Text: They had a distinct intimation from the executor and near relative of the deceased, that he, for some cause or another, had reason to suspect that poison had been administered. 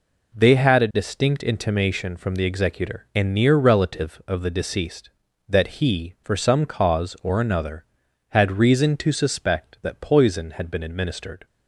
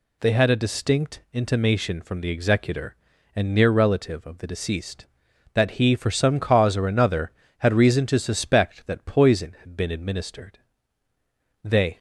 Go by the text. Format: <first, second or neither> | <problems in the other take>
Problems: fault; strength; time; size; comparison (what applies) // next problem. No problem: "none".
first | goes on to say "They"; slight; from 11.6 s on; 0.34 s long